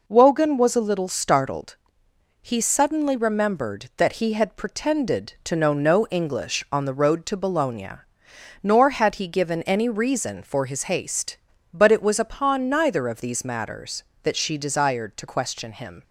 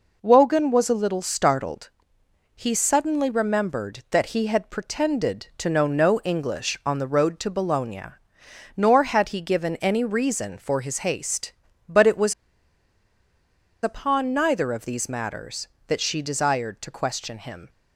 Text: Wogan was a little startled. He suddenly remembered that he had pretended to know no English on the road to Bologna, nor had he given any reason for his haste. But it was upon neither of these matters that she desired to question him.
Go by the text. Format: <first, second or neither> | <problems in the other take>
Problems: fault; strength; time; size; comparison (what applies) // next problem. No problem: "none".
first | pauses between "was" and "upon"; strong; at 12.3 s; 1.4 s long